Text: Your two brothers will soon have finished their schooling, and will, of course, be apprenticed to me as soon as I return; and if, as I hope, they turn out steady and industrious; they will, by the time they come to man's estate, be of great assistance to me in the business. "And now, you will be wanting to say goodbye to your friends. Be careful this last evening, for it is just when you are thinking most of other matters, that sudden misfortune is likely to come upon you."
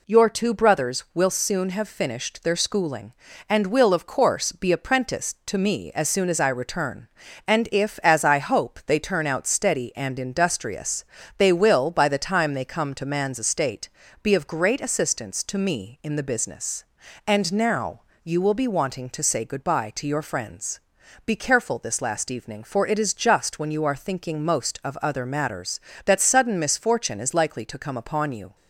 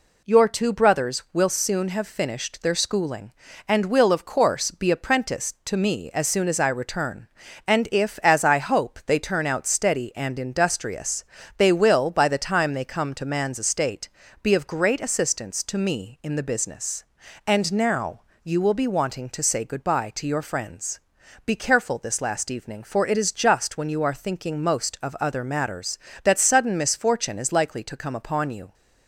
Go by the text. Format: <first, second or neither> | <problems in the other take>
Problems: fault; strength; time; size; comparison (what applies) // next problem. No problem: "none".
neither | none